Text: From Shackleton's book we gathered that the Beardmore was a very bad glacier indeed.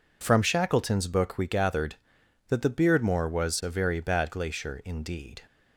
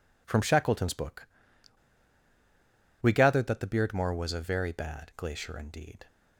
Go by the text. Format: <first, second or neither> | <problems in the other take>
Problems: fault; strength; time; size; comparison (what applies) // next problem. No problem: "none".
first | pauses between "book" and "we"; strong; at 1.2 s; 1.7 s long